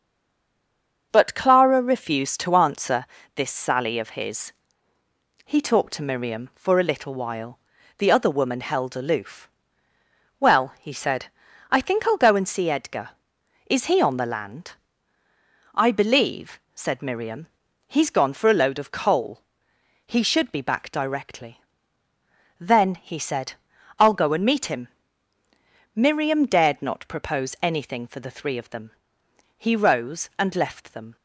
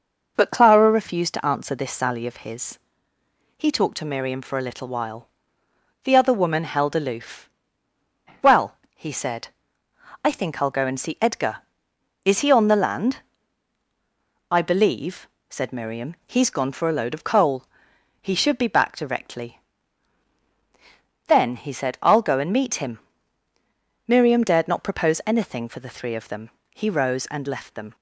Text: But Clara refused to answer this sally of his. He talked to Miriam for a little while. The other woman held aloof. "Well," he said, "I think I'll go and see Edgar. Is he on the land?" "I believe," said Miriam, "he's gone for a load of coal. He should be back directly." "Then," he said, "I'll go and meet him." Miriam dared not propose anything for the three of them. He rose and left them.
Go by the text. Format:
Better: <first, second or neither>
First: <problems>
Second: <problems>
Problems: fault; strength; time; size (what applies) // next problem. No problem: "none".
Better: second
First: stays silent before the first word; until 1.1 s; 1.1 s long // starts louder than the rest; until 2.1 s; 6.5 dB // pauses between "answer" and "this"; slight; at 3.0 s; 0.30 s long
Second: none